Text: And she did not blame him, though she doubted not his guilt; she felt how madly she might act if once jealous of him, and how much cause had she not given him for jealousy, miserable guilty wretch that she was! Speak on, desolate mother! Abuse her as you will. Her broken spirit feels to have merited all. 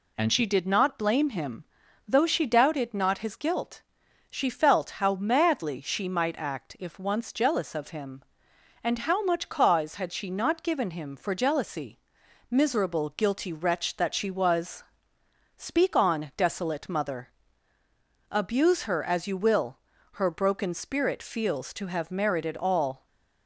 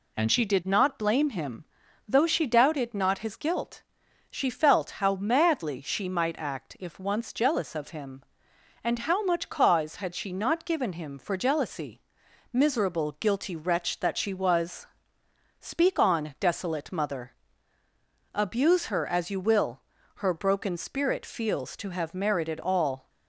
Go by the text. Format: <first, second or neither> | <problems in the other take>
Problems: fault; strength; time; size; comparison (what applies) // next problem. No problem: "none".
neither | none